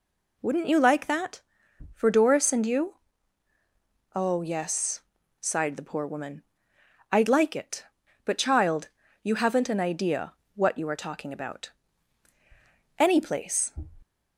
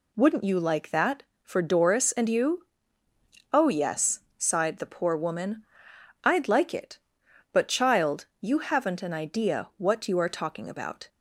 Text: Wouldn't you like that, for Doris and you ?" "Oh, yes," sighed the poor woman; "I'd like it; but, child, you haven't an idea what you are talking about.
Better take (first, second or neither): second